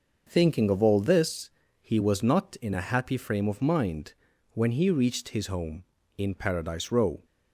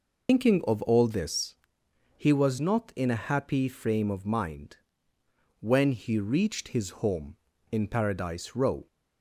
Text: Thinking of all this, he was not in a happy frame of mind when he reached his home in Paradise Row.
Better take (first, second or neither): first